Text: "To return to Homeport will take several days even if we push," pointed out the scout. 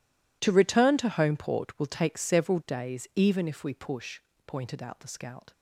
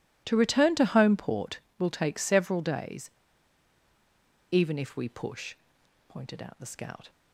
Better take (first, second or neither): first